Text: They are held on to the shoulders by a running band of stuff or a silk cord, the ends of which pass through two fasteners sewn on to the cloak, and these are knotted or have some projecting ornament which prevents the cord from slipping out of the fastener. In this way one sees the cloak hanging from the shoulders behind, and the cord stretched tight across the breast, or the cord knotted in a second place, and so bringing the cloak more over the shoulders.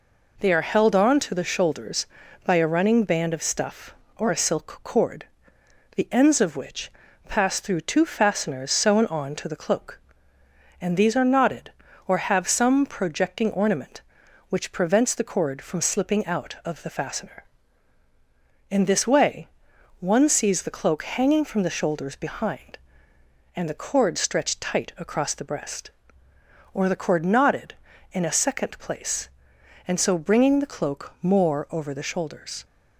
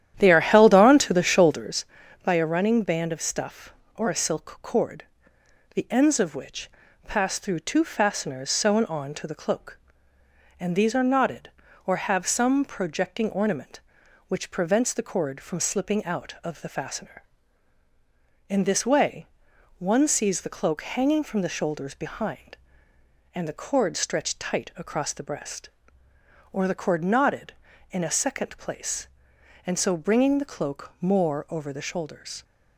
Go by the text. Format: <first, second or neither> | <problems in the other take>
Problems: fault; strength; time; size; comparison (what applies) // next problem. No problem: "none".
first | starts louder than the rest; strong; until 1.7 s; 11 dB // pauses between "which" and "pass"; at 6.6 s; 0.38 s long; also in the first // pauses between "way" and "one"; noticeable; at 19.2 s; 0.54 s long; noticeable in the first